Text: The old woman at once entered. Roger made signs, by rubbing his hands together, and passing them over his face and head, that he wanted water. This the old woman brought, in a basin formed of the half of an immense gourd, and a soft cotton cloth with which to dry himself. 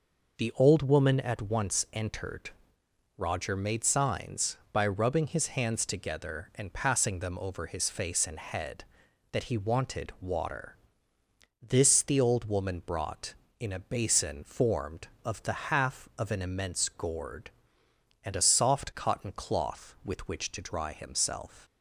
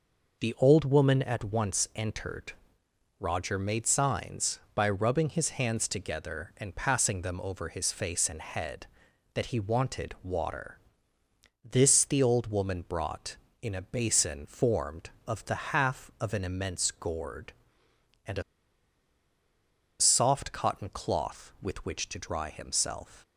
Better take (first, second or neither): first